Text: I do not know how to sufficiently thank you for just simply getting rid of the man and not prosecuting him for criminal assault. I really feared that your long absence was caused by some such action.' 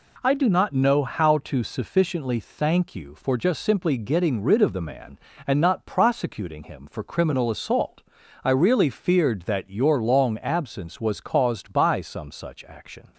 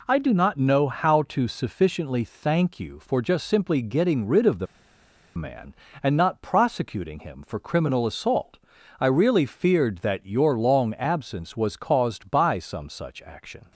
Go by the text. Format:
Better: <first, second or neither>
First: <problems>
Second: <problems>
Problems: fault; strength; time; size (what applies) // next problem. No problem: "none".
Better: first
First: none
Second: pauses between "the" and "man"; noticeable; at 4.6 s; 0.71 s long